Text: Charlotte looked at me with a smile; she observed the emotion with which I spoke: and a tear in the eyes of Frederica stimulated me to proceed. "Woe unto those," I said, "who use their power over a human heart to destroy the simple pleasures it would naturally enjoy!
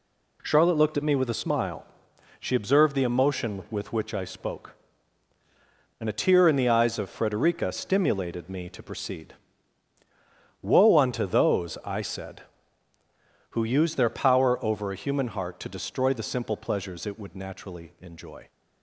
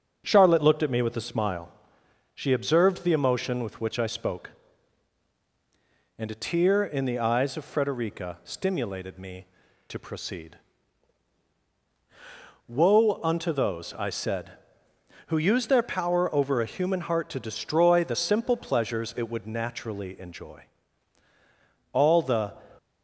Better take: first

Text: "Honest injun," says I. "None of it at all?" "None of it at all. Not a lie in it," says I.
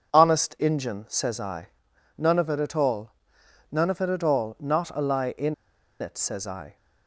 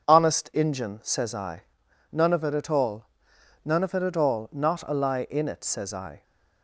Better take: second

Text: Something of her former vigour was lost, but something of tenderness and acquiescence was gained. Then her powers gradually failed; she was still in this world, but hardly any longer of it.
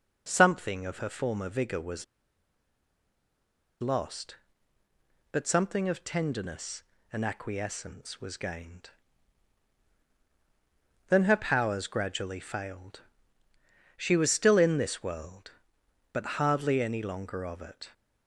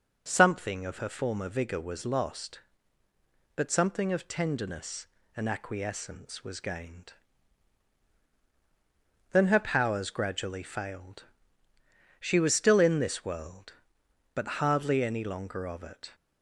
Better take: second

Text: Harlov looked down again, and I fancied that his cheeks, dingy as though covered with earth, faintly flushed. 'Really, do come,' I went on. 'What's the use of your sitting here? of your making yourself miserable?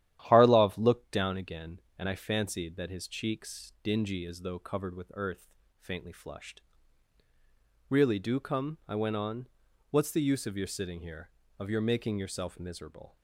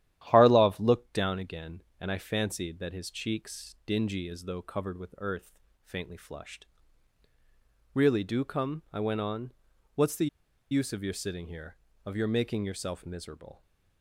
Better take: first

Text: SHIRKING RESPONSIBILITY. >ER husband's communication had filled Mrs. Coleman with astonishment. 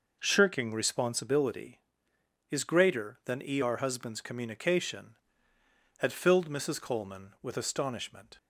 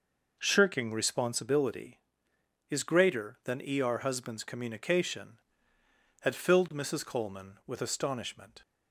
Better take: neither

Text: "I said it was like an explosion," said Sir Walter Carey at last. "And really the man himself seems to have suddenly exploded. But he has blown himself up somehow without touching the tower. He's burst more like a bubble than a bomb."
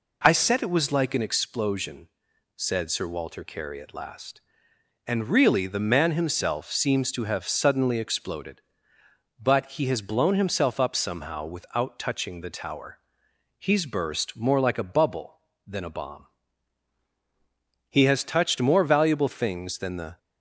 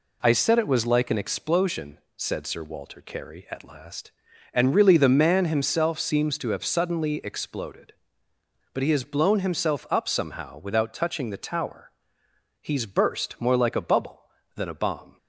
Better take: second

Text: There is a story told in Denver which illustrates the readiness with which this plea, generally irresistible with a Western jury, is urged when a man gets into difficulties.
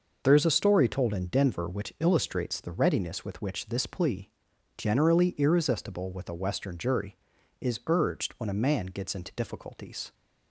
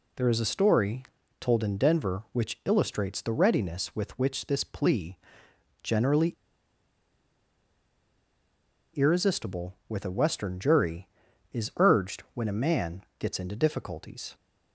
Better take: first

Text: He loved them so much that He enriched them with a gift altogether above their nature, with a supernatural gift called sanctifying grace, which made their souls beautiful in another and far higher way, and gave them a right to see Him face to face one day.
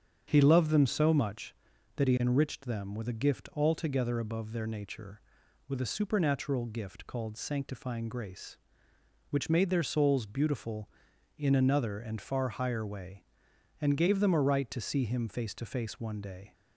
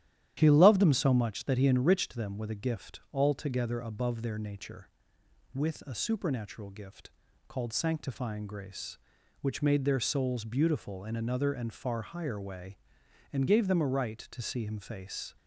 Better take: first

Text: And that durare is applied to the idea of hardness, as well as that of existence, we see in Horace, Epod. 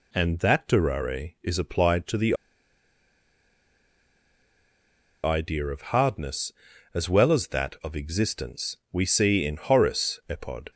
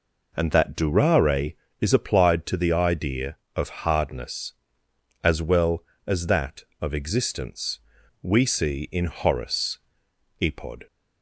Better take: second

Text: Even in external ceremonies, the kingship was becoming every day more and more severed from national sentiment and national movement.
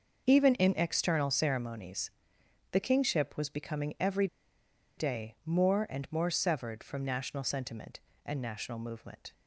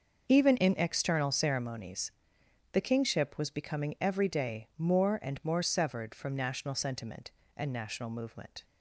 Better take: second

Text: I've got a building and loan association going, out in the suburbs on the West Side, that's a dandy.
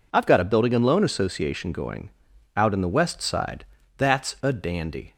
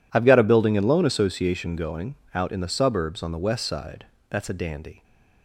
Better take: second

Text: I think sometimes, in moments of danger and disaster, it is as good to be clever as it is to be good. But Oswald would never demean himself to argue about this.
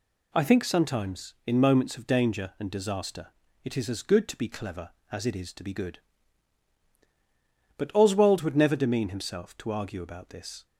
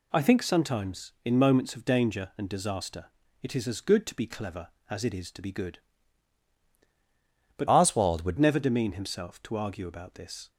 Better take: first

